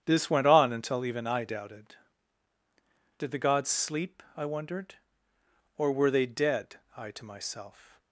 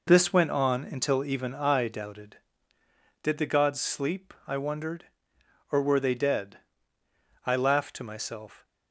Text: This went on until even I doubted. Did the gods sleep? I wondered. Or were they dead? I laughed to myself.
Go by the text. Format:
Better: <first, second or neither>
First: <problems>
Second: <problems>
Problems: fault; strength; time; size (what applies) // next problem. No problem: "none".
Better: second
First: starts louder than the rest; strong; until 1.0 s; 8.5 dB // skips "laughed"; at 7.1 s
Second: none